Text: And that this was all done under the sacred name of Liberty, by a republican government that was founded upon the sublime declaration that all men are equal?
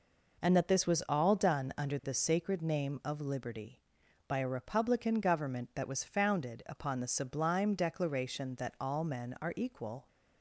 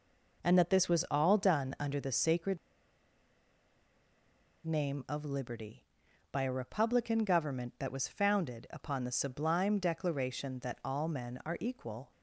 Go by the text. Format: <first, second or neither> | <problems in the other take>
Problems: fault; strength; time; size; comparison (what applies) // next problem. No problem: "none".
first | pauses between "sacred" and "name"; strong; at 2.5 s; 2.0 s long